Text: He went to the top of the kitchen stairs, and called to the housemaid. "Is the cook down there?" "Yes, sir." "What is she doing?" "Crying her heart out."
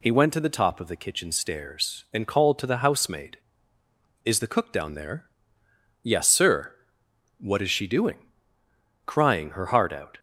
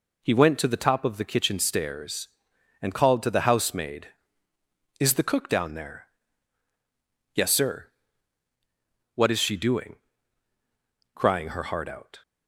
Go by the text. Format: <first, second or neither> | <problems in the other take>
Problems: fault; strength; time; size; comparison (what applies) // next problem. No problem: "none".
neither | none